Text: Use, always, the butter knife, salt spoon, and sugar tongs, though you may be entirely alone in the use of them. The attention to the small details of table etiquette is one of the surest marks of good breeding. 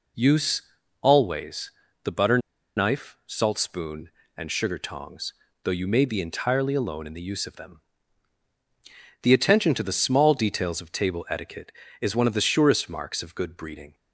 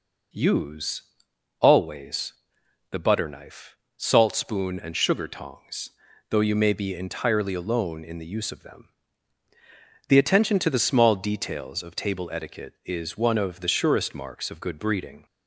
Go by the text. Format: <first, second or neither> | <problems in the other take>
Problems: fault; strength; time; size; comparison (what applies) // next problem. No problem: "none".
second | pauses between "butter" and "knife"; at 2.3 s; 0.38 s long